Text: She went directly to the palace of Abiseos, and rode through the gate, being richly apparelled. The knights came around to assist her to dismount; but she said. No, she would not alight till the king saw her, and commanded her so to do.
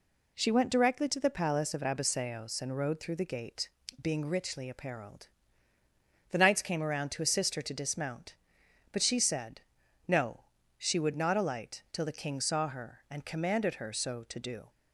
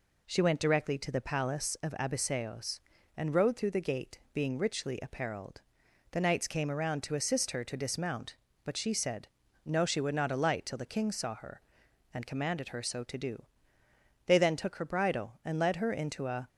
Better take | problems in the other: first | goes on to say "They then took her bridle and led her into a"; strong; from 14.2 s on; 2.2 s long

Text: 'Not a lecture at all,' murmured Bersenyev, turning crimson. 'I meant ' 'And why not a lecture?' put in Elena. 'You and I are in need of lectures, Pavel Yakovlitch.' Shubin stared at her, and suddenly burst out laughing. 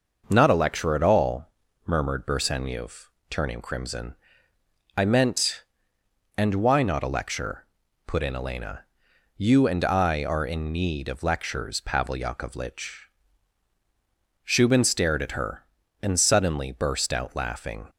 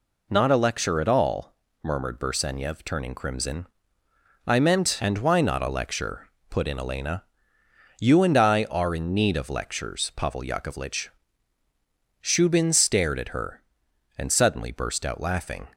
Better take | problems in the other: neither | none

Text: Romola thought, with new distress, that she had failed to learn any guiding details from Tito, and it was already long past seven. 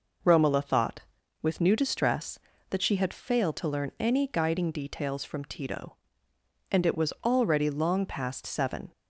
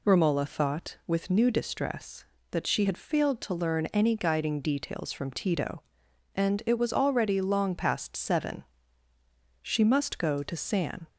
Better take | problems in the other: first | goes on to say "She must go to San"; from 9.6 s on; 1.3 s long

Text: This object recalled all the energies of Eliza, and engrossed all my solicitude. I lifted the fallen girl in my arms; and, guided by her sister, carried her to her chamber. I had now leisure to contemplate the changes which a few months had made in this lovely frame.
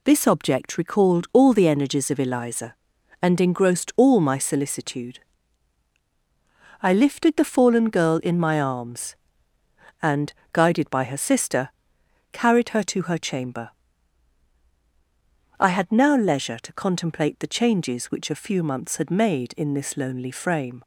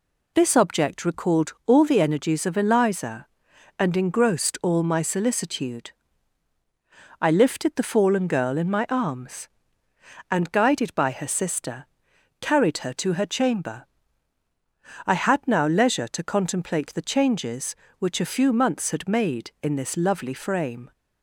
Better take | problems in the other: second | says "lonely" for "lovely"; at 19.9 s

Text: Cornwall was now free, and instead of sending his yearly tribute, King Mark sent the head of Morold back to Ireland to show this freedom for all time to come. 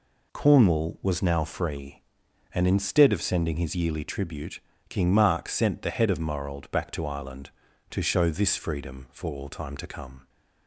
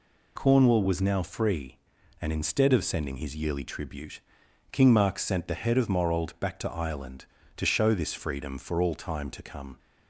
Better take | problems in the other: neither | none

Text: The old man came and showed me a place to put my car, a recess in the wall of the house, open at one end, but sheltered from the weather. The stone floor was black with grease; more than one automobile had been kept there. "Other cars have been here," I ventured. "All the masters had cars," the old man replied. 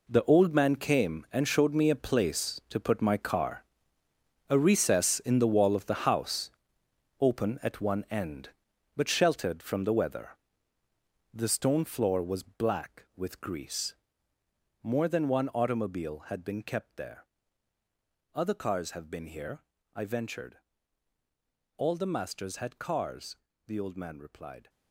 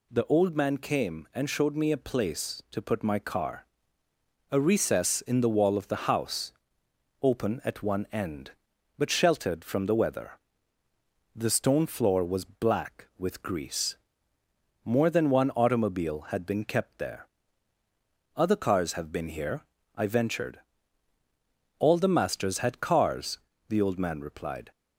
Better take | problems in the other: second | gets quieter; strong; throughout; 12.5 dB

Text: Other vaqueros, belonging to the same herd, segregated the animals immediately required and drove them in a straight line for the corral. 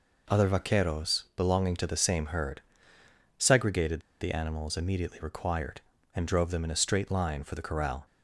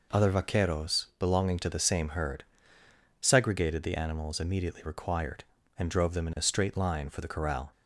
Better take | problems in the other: second | pauses between "segregated" and "the"; slight; at 3.9 s; 0.21 s long

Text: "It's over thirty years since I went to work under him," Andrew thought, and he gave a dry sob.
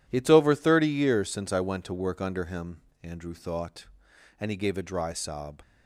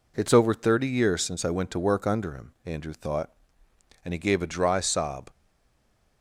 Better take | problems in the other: first | stays silent after the last word; slight; from 5.2 s on; 1.0 s long

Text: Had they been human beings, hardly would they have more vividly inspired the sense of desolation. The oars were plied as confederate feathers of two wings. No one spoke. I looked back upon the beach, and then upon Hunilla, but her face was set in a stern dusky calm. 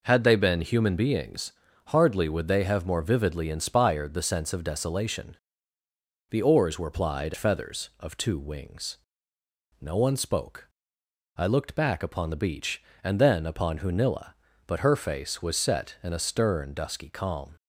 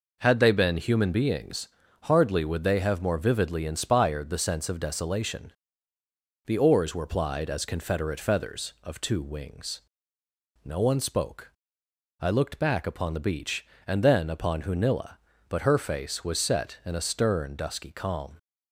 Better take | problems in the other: second | skips "as confederate"; at 7.3 s

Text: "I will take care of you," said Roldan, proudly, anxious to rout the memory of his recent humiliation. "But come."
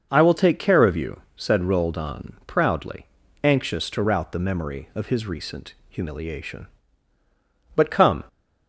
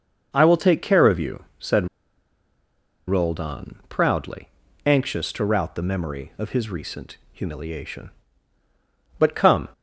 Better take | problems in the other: first | starts louder than the rest; noticeable; until 1.3 s; 6 dB; noticeable in the first // pauses between "said" and "Roldan"; at 1.8 s; 1.2 s long // pauses between "recent" and "humiliation"; slight; at 7.1 s; 0.16 s long; slight in the first

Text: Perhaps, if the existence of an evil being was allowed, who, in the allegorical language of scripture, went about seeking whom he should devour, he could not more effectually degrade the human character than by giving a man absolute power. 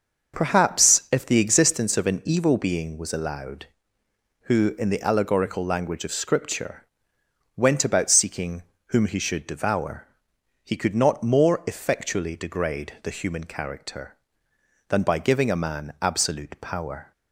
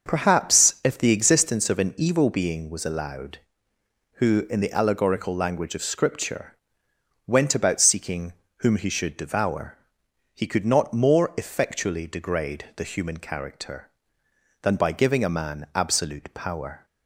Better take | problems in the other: neither | starts louder than the rest; the same in both // pauses between "seeking" and "whom"; slight; the same in both

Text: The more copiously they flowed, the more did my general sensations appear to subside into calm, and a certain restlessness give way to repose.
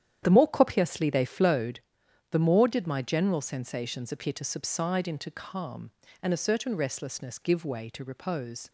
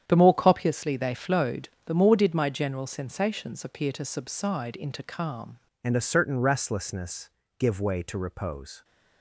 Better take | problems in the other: first | starts louder than the rest; strong; until 1.1 s; 9 dB; strong in the first // changes voice at "and"; from 5.8 s on; 3.0 s long // pauses between "restlessness" and "give"; slight; at 7.2 s; 0.28 s long

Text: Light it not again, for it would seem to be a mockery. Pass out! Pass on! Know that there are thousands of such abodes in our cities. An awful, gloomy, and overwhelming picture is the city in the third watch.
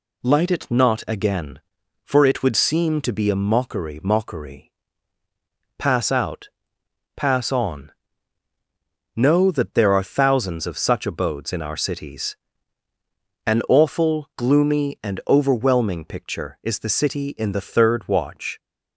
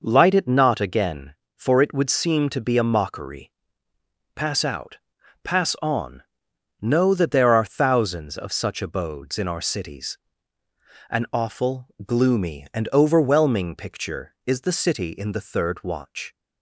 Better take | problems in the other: second | says "mockery" twice; at 4.0 s

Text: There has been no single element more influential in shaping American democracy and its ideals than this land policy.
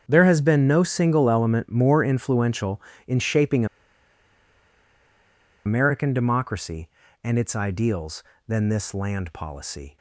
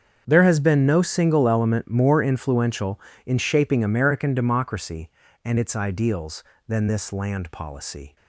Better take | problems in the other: second | starts louder than the rest; until 1.0 s; 7 dB; also in the second // pauses between "shaping" and "American"; strong; at 3.6 s; 2.0 s long

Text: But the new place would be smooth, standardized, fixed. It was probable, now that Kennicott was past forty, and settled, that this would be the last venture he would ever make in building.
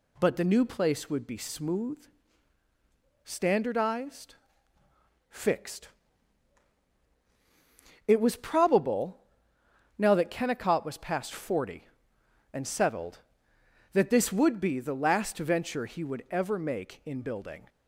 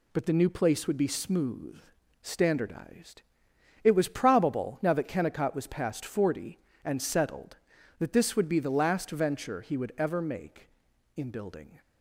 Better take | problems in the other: first | skips "fixed"; at 3.5 s

